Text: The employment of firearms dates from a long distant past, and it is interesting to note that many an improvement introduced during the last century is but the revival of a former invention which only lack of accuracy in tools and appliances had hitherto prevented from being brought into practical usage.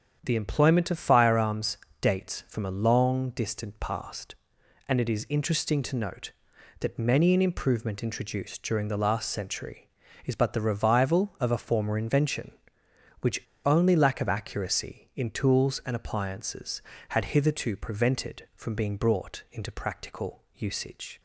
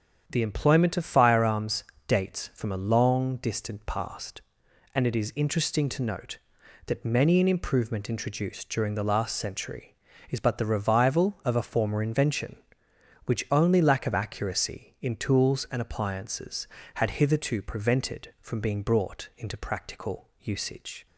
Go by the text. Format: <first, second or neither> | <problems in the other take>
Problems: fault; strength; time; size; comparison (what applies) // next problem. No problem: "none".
second | starts louder than the rest; strong; until 1.2 s; 8 dB; strong in the second // pauses between "firearms" and "dates"; slight; at 1.7 s; 0.24 s long; slight in the second // pauses between "which" and "only"; slight; at 13.4 s; 0.24 s long